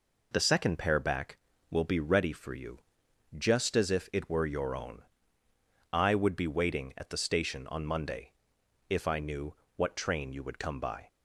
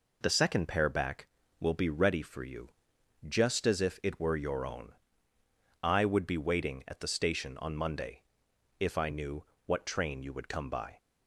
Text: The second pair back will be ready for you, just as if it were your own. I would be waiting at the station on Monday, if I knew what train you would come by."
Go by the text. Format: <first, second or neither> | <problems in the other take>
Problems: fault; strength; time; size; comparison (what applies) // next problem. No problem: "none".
neither | pauses between "knew" and "what"; slight; the same in both